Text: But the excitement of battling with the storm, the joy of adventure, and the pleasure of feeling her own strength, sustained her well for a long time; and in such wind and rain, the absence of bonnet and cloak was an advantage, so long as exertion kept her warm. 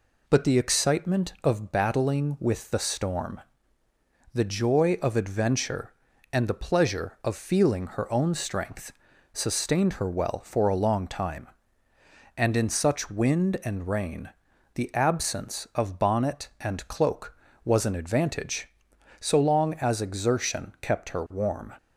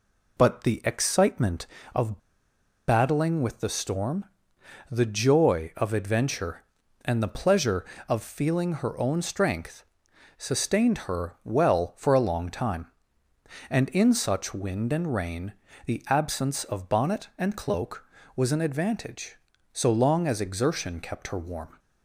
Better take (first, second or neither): first